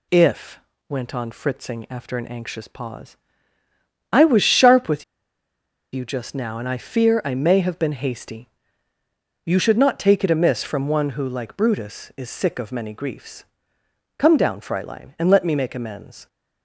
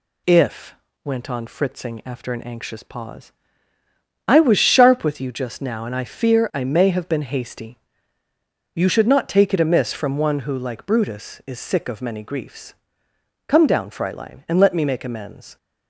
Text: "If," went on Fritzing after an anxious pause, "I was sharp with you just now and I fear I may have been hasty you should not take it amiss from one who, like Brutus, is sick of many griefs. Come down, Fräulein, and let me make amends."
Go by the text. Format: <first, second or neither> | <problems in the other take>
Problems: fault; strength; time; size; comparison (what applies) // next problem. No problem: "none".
second | pauses between "with" and "you"; noticeable; at 5.0 s; 0.89 s long // pauses between "hasty" and "you"; noticeable; at 8.4 s; 0.96 s long; noticeable in the second